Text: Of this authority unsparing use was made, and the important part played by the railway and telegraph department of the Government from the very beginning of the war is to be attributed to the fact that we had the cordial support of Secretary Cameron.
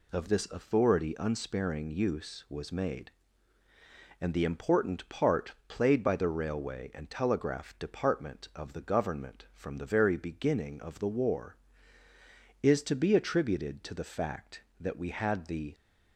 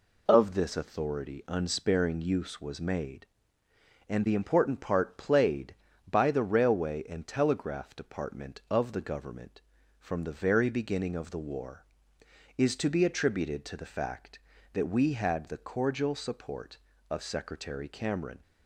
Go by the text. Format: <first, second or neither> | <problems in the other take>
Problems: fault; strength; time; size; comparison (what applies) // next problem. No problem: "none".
second | stops before "cordial support of Secretary Cameron"; at 15.7 s